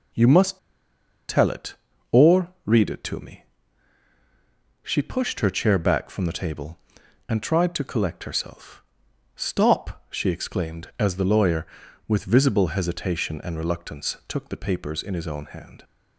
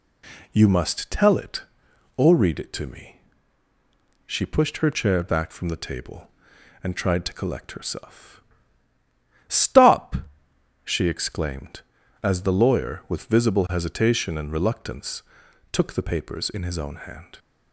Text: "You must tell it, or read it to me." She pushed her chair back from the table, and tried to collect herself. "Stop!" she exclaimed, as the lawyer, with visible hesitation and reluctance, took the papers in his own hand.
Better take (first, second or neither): second